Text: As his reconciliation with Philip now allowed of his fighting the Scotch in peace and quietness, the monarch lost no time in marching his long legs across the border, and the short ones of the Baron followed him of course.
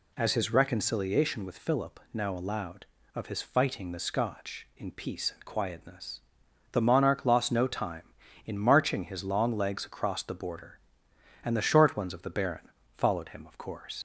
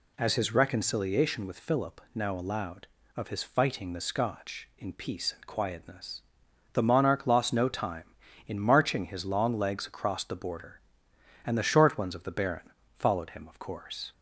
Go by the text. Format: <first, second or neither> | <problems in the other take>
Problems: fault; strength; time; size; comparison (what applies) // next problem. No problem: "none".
second | pauses between "Baron" and "followed"; slight; at 12.6 s; 0.26 s long; slight in the second // leaves "course" unfinished; at 13.9 s; 85 ms